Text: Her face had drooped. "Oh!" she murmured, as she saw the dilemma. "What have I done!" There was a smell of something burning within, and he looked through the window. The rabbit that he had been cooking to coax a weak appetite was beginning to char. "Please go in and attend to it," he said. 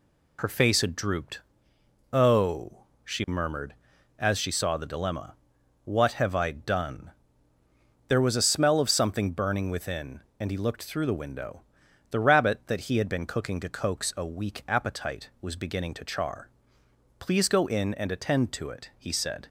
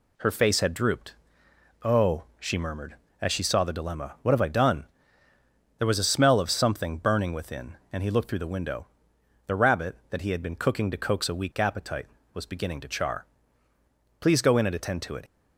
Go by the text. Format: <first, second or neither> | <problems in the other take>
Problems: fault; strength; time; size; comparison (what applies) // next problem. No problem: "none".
first | stops before "he said"; at 15.2 s